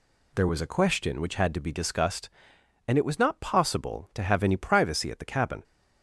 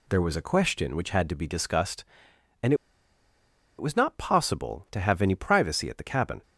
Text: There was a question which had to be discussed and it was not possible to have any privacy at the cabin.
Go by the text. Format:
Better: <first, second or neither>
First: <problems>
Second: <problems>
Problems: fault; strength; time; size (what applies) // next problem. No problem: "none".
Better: first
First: none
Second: pauses between "and" and "it"; at 2.7 s; 1.0 s long